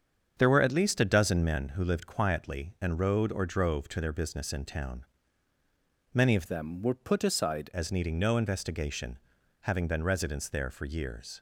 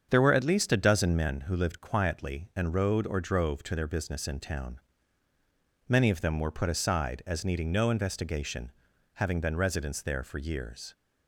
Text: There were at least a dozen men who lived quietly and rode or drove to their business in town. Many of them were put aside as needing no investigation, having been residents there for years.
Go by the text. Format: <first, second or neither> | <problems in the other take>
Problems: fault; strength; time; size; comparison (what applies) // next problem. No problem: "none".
second | starts louder than the rest; strong; until 1.3 s; 7.5 dB; strong in the second // changes voice from "them" to "aside"; from 6.4 to 7.6 s; 1.2 s long